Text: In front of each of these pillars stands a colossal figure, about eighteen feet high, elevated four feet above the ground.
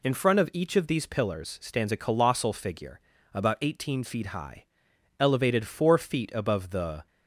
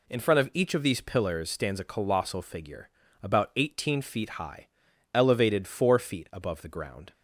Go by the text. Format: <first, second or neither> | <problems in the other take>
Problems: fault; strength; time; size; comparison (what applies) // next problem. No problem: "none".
second | stops before "ground"; at 7.0 s